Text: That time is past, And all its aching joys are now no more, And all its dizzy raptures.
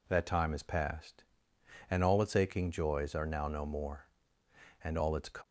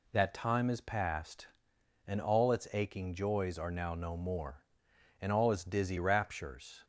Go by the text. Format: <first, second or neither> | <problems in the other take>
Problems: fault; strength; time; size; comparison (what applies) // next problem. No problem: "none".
second | stops before "dizzy raptures"; at 5.4 s